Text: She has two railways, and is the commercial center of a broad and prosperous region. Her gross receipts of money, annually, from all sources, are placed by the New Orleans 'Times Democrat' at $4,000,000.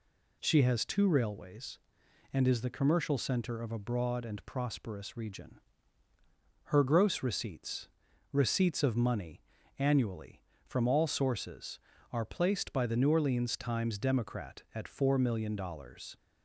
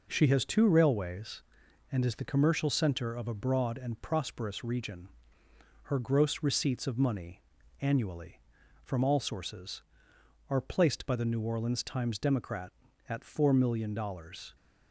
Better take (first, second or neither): second